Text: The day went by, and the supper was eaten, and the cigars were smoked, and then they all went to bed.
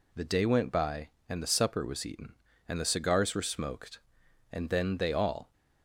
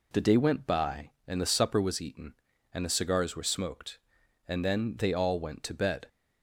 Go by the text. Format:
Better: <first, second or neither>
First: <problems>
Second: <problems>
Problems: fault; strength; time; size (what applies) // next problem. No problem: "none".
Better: second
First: stops before "went to bed"; at 5.5 s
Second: none